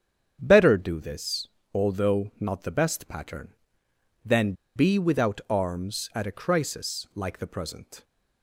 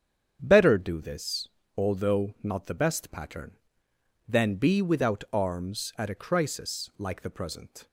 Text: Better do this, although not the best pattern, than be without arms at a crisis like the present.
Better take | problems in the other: second | starts louder than the rest; strong; until 1.4 s; 8 dB; strong in the second // pauses between "than" and "be"; slight; at 4.5 s; 0.22 s long

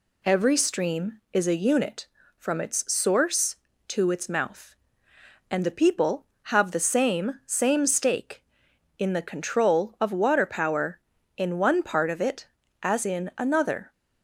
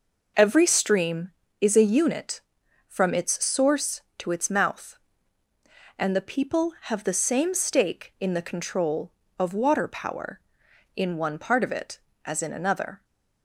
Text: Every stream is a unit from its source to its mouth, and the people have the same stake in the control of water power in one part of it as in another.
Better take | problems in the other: second | says "same" twice; at 7.4 s

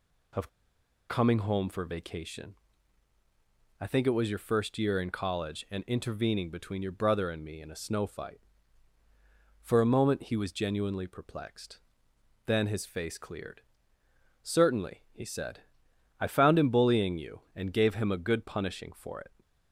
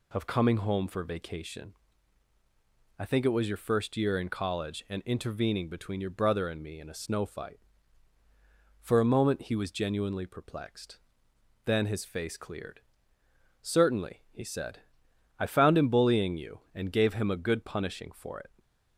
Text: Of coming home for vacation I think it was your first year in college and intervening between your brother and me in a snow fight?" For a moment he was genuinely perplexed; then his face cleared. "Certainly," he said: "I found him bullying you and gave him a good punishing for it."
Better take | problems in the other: second | pauses between "Of" and "coming"; noticeable; at 0.4 s; 0.61 s long // pauses between "vacation" and "I"; strong; at 2.5 s; 1.2 s long; strong in the second

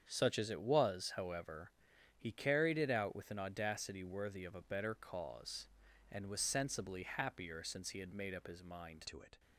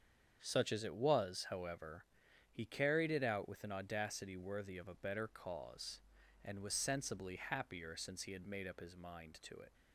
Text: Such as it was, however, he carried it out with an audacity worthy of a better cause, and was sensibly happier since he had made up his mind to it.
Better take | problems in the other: second | starts louder than the rest; strong; until 1.0 s; 7.5 dB; strong in the second // changes voice at "to"; from 9.0 s on; 0.3 s long

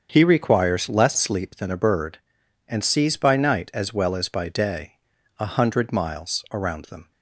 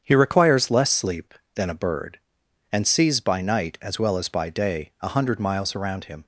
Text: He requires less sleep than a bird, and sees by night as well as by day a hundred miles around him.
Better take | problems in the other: second | starts louder than the rest; strong; until 1.1 s; 7 dB; strong in the second // pauses between "day" and "a"; at 4.9 s; 0.42 s long // says "them" for "him"; at 6.8 s

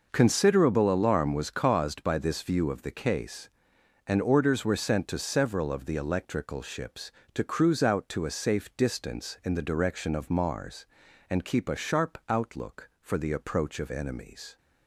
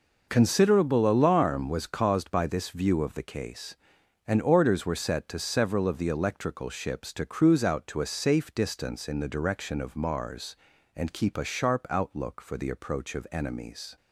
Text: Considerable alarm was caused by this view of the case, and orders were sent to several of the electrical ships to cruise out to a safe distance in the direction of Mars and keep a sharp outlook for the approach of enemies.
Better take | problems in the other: first | says "set" for "sent"; at 4.9 s

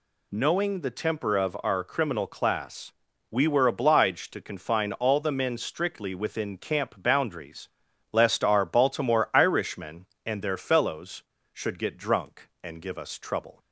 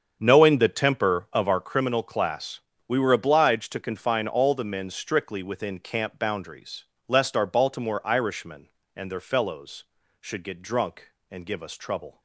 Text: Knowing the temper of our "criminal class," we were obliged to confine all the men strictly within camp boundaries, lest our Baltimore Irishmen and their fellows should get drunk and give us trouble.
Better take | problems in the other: first | starts louder than the rest; strong; until 1.8 s; 7.5 dB

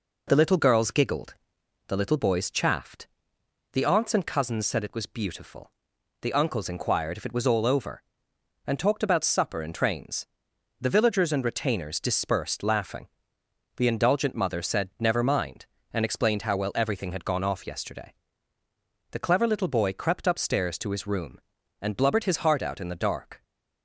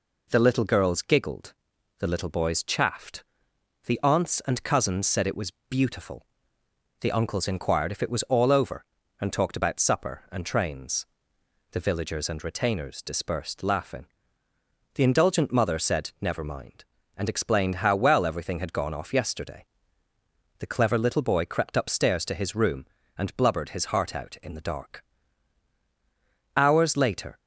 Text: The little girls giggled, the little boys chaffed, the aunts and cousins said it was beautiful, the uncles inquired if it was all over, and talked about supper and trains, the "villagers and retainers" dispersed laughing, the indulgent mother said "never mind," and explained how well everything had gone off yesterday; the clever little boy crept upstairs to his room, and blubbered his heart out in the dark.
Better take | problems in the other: first | pauses between "was" and "beautiful"; slight; at 5.5 s; 0.18 s long // goes on to say "Hours later"; noticeable; from 26.5 s on; 0.84 s long

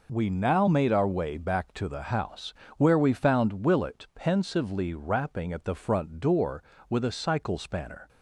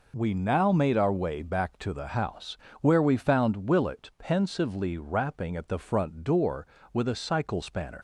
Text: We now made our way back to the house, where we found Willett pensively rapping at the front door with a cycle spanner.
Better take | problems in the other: first | leaves "spanner" unfinished; at 7.9 s; 90 ms

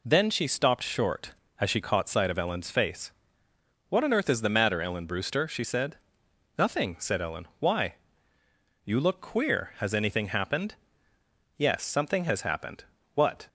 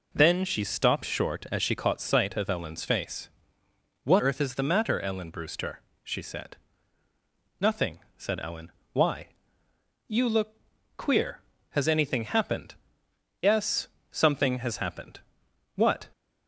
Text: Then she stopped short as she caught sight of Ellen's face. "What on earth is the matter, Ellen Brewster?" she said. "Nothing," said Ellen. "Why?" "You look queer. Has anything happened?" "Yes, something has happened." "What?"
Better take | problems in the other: first | skips "on"; at 4.1 s // pauses between "look" and "queer"; at 10.5 s; 0.40 s long

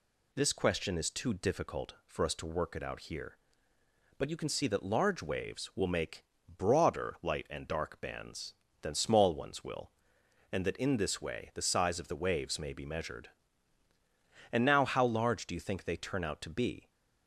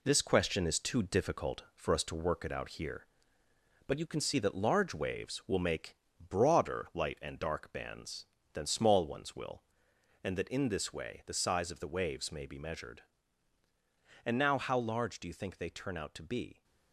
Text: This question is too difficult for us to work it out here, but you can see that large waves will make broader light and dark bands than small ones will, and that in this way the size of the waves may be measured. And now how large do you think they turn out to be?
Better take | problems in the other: first | gets quieter; throughout; 6.5 dB // pauses between "make" and "broader"; slight; at 5.9 s; 0.32 s long; slight in the first

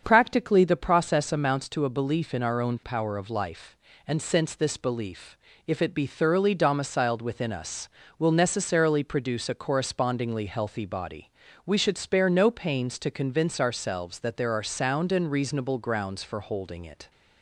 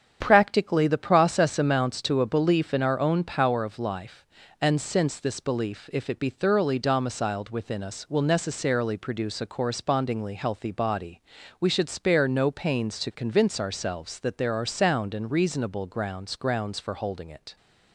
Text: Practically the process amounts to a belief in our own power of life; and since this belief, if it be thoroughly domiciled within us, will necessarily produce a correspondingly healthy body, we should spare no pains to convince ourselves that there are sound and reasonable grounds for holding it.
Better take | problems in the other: first | starts louder than the rest; strong; until 1.2 s; 8.5 dB; also in the first // says "grounds" twice; at 16.3 s

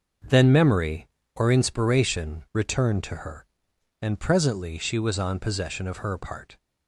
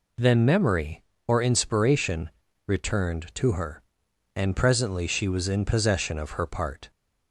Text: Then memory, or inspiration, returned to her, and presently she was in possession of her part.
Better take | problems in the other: second | starts louder than the rest; noticeable; until 1.4 s; 6 dB // says "on" for "in"; at 5.1 s

